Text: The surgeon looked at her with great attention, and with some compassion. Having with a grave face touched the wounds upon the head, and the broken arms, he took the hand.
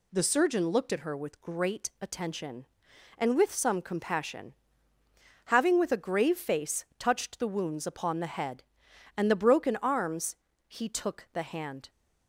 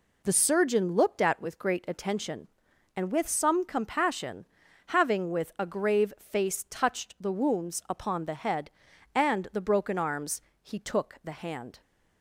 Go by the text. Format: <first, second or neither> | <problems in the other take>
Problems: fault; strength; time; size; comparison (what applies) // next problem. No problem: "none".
first | skips "her"; at 1.4 s